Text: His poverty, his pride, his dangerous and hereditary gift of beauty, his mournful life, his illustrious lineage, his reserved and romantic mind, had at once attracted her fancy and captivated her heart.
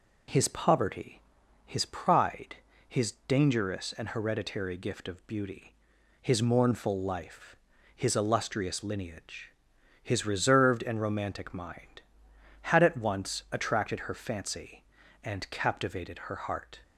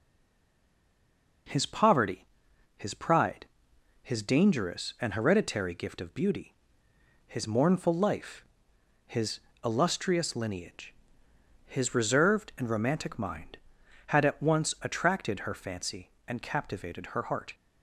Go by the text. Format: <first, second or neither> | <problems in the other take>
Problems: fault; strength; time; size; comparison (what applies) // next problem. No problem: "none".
first | stays silent before the first word; noticeable; until 1.4 s; 1.4 s long // pauses between "his" and "illustrious"; slight; at 9.3 s; 0.24 s long